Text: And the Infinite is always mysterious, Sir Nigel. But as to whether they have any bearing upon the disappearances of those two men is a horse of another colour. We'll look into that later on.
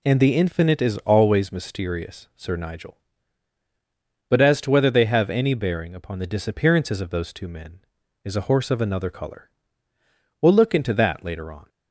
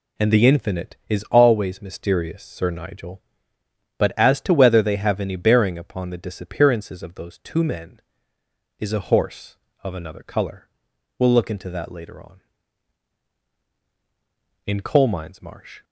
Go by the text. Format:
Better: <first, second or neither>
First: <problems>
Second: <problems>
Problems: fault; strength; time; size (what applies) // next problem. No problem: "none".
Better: first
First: none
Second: goes on to say "In coal mines marsh"; noticeable; from 14.6 s on; 1.1 s long